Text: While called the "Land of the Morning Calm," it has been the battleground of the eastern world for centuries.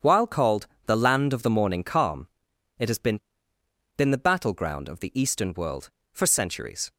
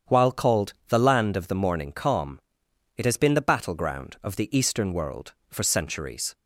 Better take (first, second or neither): second